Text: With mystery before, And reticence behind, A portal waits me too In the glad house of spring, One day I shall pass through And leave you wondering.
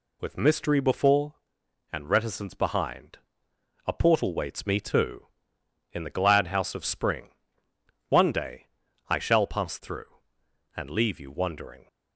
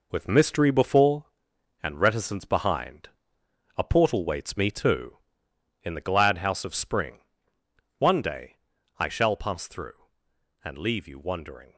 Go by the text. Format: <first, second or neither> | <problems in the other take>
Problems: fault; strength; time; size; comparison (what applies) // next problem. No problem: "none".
first | gets quieter; strong; throughout; 7.5 dB // pauses between "day" and "I"; at 8.5 s; 0.44 s long; also in the first